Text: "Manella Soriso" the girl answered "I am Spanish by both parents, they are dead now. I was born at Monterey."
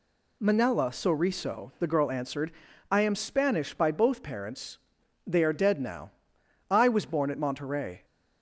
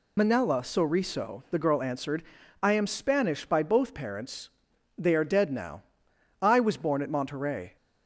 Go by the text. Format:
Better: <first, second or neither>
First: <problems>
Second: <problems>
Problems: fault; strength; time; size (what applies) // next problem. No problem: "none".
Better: first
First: pauses between "answered" and "I"; at 2.5 s; 0.40 s long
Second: loses the start of "Manella"; at 0.1 s; 50 ms // pauses between "answered" and "I"; at 2.2 s; 0.40 s long